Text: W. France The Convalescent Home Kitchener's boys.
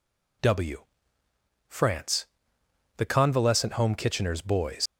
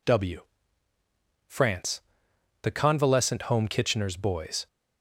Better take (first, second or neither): second